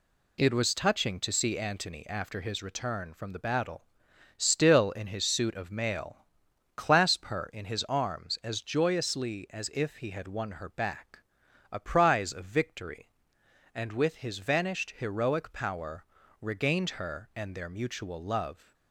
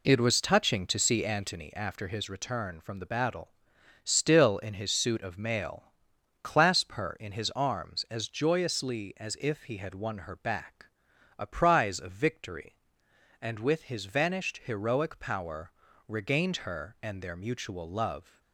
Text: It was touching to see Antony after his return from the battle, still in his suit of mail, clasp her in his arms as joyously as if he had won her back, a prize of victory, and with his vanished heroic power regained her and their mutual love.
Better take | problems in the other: first | starts louder than the rest; slight; until 1.6 s; 3 dB // pauses between "power" and "regained"; slight; at 15.7 s; 0.34 s long; slight in the first

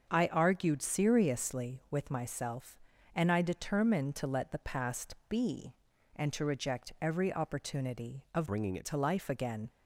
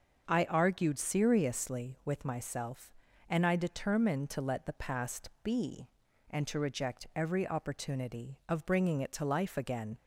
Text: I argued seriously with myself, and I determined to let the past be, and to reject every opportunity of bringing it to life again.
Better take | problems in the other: second | starts louder than the rest; until 1.1 s; 6.5 dB; also in the second // changes voice from "bringing" to "it"; from 8.4 to 8.8 s; 0.4 s long

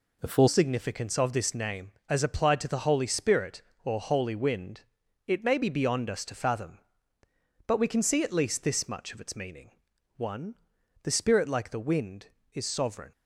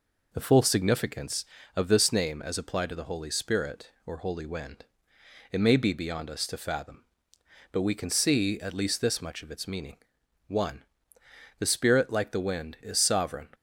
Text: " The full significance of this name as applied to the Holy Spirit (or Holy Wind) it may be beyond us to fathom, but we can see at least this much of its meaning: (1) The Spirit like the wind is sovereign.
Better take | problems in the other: second | changes voice at "significance"; from 0.4 s on; 12.7 s long

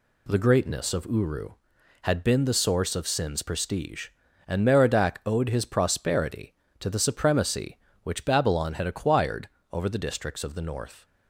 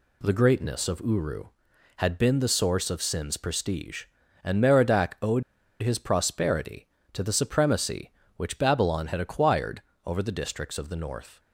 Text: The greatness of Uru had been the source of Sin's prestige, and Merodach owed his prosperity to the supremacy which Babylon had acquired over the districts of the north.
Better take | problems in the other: first | pauses between "owed" and "his"; at 5.4 s; 0.40 s long // pauses between "acquired" and "over"; slight; at 9.8 s; 0.24 s long; slight in the first

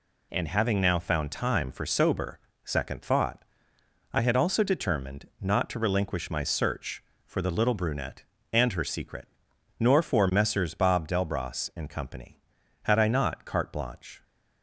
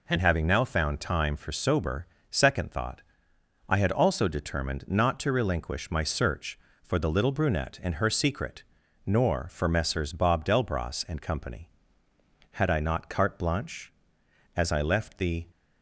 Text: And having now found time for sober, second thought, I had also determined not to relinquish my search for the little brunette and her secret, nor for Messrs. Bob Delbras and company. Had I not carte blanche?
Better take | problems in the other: first | goes on to say "As I left the"; noticeable; from 14.5 s on; 0.90 s long

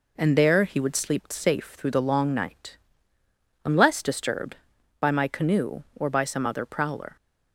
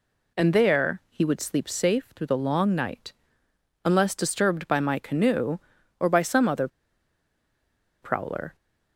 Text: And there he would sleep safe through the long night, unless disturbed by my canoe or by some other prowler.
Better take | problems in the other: first | pauses between "other" and "prowler"; strong; at 6.6 s; 1.3 s long

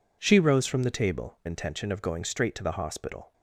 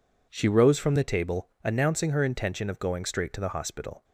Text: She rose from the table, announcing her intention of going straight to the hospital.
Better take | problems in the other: second | skips "announcing her"; at 1.4 s

